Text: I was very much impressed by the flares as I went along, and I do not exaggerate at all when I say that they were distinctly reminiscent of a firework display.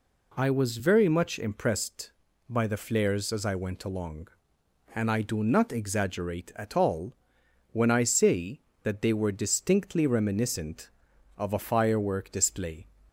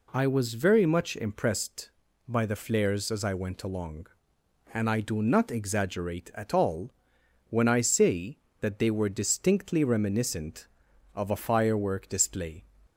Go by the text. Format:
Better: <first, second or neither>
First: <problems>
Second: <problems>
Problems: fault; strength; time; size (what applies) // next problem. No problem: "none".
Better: neither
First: pauses between "all" and "when"; noticeable; at 7.1 s; 0.58 s long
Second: pauses between "all" and "when"; noticeable; at 6.9 s; 0.58 s long